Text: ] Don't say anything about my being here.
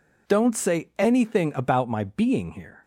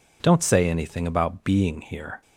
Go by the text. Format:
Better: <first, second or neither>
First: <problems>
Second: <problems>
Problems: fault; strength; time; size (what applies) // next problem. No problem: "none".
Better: first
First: none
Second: skips "my"; at 1.4 s